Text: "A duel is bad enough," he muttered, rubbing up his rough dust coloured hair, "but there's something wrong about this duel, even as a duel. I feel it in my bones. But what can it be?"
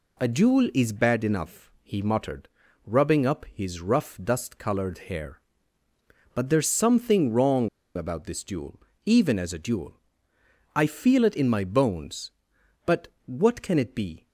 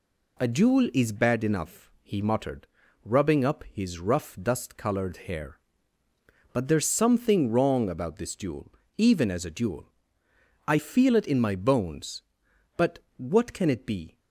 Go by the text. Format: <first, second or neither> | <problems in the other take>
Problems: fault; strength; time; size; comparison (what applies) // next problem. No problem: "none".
second | pauses between "coloured" and "hair"; slight; at 4.9 s; 0.16 s long; slight in the second // pauses between "wrong" and "about"; slight; at 7.6 s; 0.26 s long // pauses between "But" and "what"; slight; at 13.0 s; 0.18 s long; slight in the second